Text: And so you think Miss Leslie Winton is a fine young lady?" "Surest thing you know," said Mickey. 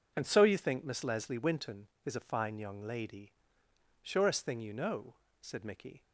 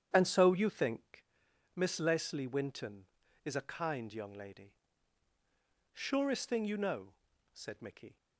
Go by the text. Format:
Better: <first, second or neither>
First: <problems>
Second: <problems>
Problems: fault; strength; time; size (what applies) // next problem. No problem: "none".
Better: first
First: none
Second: starts louder than the rest; strong; until 1.1 s; 9 dB // pauses between "think" and "Miss"; noticeable; at 1.2 s; 0.50 s long // says "kind" for "fine"; at 3.6 s